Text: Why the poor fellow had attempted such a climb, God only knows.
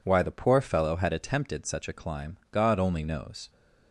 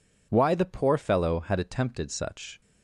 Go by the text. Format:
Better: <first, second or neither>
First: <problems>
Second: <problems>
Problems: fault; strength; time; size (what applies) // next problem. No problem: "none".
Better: first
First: none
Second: stops before "a climb God only knows"; at 2.6 s